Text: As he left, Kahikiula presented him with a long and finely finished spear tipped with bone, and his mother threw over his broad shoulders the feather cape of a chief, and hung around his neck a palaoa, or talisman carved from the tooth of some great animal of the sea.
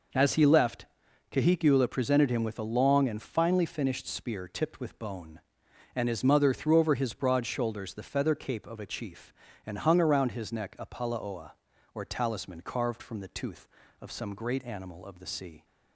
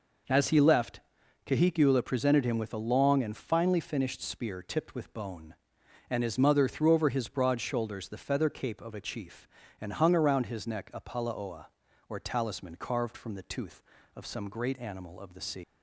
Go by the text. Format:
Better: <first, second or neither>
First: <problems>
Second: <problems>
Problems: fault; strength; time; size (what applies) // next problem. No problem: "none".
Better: first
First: none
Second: leaves "sea" unfinished; at 15.6 s; 155 ms